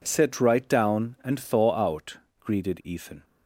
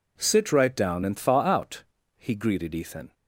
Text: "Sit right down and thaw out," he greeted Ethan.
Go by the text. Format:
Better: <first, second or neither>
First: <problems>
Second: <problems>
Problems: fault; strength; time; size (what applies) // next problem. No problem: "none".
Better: second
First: skips "he"; at 2.2 s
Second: none